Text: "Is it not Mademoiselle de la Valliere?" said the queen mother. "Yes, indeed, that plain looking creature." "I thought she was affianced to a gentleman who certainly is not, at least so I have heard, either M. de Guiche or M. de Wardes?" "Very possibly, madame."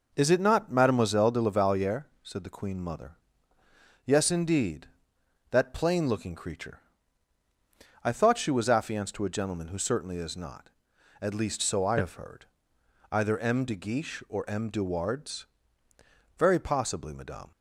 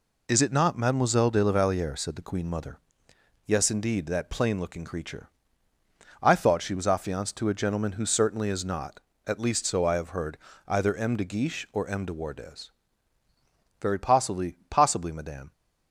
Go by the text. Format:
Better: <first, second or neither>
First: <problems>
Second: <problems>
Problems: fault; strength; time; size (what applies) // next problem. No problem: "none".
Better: first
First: none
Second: says "possibly" twice; at 14.7 s